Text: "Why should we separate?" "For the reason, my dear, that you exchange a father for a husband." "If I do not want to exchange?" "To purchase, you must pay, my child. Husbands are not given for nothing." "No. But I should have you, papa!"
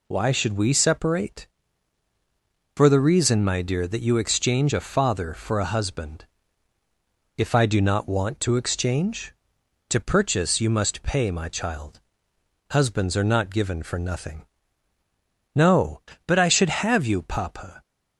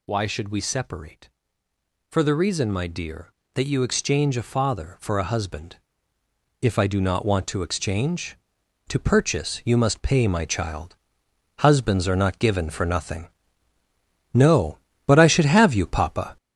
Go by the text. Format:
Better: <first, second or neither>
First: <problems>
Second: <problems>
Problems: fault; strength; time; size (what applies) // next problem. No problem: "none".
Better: first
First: none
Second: gets louder; throughout; 6.5 dB